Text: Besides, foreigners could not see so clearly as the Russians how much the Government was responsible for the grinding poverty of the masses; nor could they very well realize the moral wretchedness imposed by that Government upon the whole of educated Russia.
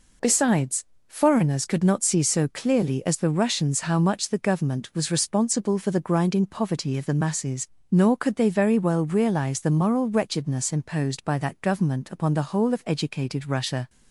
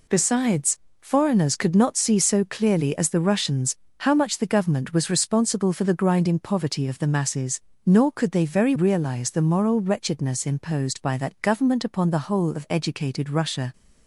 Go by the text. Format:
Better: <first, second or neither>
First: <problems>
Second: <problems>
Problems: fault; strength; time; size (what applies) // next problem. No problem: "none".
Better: first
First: none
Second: pauses between "Russians" and "how"; slight; at 3.7 s; 0.24 s long // skips "well"; at 8.7 s